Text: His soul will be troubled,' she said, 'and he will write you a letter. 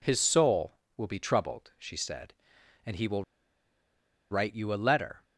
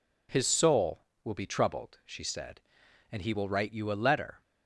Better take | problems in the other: second | pauses between "will" and "write"; at 3.2 s; 1.0 s long

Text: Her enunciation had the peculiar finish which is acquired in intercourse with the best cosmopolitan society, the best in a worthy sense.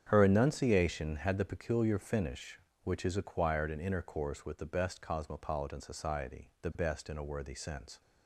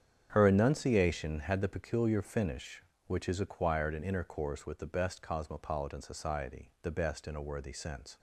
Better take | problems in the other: neither | starts louder than the rest; strong; the same in both

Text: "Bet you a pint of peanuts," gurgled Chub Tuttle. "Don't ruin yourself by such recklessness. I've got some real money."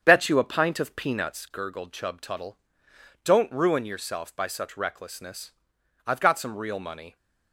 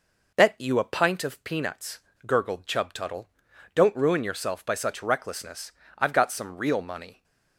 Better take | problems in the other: second | starts louder than the rest; strong; until 1.5 s; 8 dB

